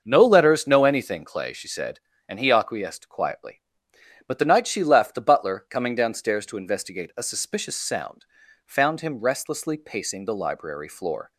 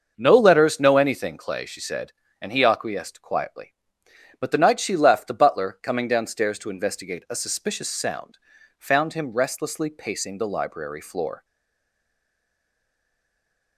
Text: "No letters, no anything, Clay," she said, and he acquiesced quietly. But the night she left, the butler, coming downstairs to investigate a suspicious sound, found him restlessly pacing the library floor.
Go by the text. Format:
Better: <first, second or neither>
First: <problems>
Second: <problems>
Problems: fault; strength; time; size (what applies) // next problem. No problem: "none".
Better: first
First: starts louder than the rest; until 1.0 s; 6.5 dB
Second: starts louder than the rest; until 1.1 s; 6.5 dB // stays silent after the last word; from 11.4 s on; 2.3 s long